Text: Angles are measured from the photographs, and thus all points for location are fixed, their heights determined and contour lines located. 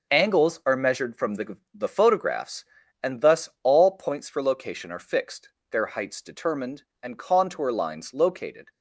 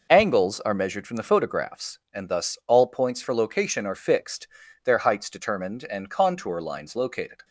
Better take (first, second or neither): second